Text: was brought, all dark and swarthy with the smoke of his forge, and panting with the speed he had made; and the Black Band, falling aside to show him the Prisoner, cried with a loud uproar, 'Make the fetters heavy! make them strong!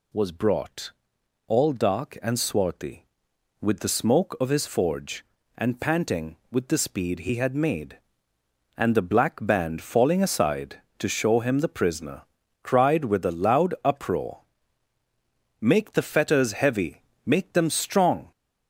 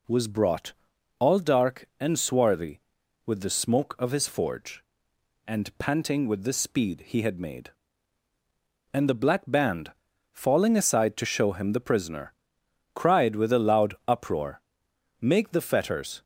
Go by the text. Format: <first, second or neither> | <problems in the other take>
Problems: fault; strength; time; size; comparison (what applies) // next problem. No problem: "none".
first | stops before "heavy make them strong"; at 16.2 s